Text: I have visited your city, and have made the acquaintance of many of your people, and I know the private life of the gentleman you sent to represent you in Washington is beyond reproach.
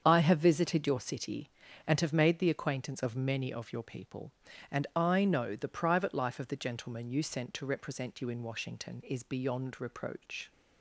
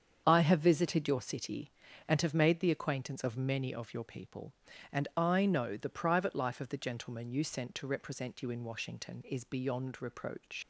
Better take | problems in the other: first | starts louder than the rest; strong; until 1.2 s; 7.5 dB; strong in the first // leaves "reproach" unfinished; at 10.6 s; 90 ms

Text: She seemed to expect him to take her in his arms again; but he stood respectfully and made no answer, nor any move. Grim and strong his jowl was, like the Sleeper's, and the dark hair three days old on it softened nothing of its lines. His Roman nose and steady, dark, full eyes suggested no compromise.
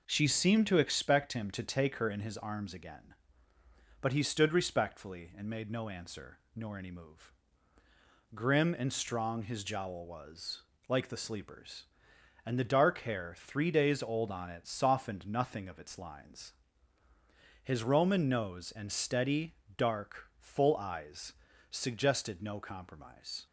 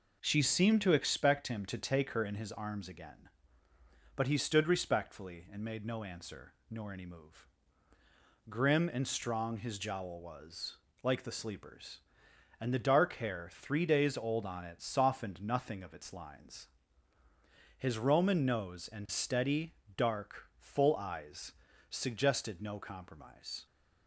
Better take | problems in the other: neither | pauses between "eyes" and "suggested"; the same in both

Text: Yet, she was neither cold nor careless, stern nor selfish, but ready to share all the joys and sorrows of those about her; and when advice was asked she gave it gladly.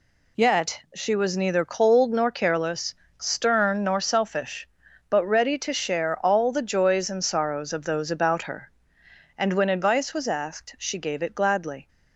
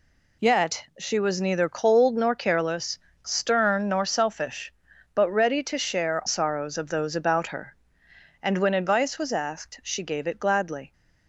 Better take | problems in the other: first | skips "all the joys and"; at 6.2 s

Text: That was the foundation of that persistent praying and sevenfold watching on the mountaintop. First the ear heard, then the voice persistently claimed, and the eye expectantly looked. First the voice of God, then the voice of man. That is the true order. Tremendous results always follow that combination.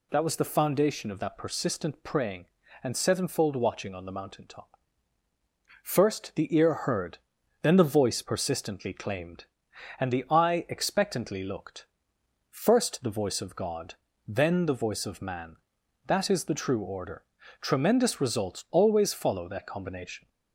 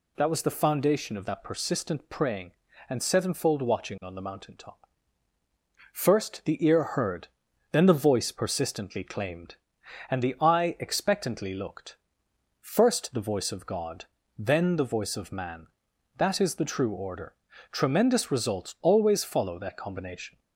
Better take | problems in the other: neither | none

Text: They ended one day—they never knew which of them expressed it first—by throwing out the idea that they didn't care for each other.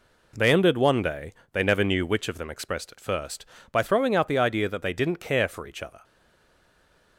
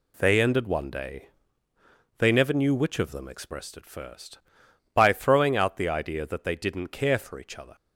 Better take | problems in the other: second | stays silent after the last word; from 6.0 s on; 1.1 s long

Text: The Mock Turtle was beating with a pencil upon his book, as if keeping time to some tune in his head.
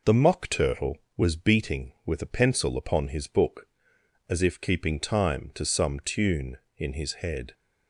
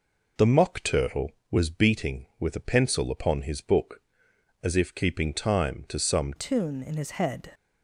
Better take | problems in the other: first | changes voice at "tune"; from 6.3 s on; 1.2 s long

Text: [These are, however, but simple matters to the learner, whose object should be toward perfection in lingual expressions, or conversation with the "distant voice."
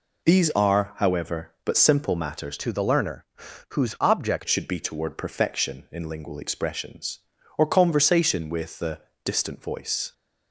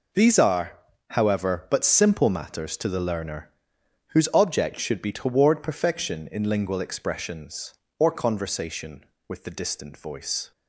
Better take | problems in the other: second | changes voice from "to" to "object"; from 2.5 to 4.4 s; 1.9 s long // pauses between "the" and "distant"; slight; at 9.0 s; 0.24 s long

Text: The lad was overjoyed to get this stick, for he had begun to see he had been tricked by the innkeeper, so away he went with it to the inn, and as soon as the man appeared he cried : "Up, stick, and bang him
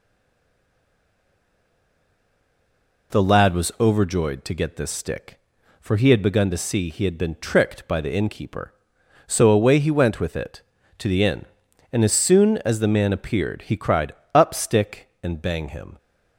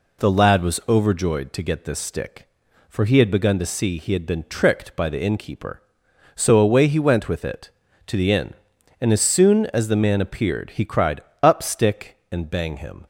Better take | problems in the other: second | stays silent before the first word; strong; until 3.1 s; 3.1 s long

